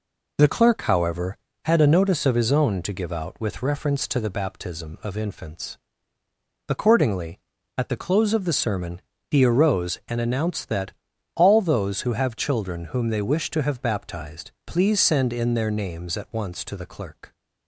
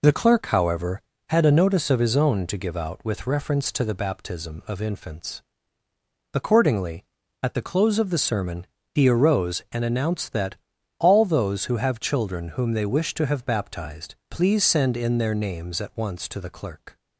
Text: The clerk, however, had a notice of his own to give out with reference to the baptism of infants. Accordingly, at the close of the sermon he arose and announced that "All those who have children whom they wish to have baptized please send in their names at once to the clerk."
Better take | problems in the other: neither | pauses between "sermon" and "he"; slight; the same in both // pauses between "that" and "All"; the same in both

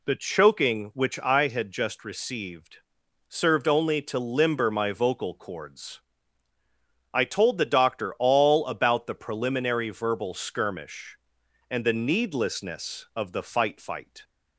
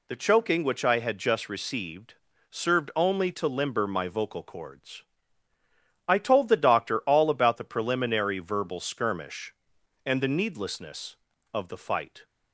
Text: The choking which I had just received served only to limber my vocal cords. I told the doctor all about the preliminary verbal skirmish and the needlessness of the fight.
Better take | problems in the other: second | pauses between "received" and "served"; noticeable; at 2.7 s; 0.52 s long; slight in the second // says "fight" twice; at 13.7 s

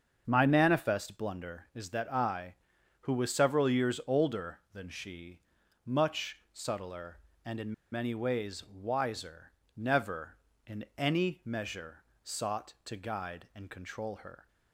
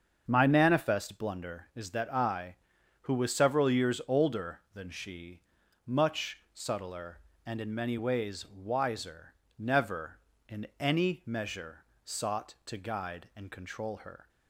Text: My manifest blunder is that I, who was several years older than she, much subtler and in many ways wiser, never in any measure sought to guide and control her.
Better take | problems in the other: second | starts louder than the rest; until 1.2 s; 7 dB; also in the second // pauses between "in" and "many"; slight; at 7.7 s; 0.19 s long // pauses between "measure" and "sought"; slight; at 12.0 s; 0.22 s long; slight in the second

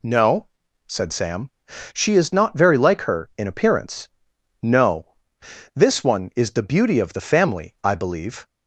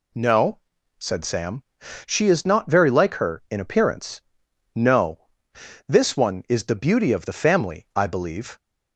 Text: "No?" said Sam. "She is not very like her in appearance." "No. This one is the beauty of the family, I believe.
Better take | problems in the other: neither | none

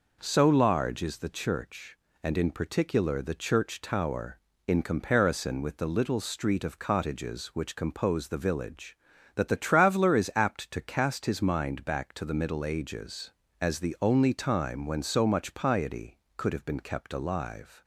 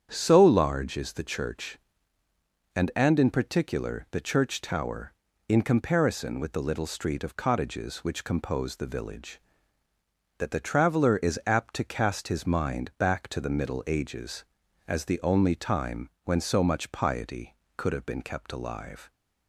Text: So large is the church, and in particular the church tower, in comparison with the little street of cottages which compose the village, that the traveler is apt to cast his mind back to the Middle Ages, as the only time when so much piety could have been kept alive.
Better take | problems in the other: first | starts louder than the rest; strong; until 1.1 s; 8.5 dB // says "and" twice; at 2.9 s // pauses between "time" and "when"; slight; at 16.0 s; 0.16 s long

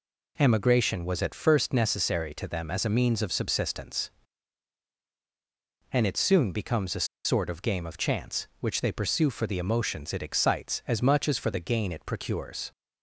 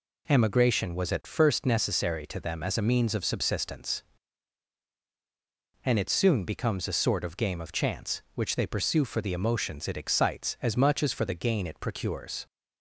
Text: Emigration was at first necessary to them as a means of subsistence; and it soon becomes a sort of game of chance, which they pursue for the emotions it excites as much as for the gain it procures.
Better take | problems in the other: second | pauses between "a" and "sort"; slight; at 7.0 s; 0.19 s long

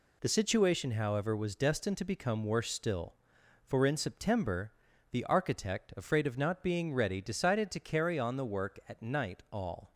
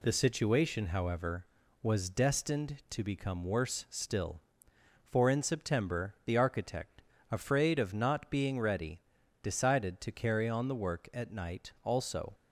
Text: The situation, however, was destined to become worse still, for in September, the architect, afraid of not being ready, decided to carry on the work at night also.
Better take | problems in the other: second | says "all" for "also"; at 9.5 s

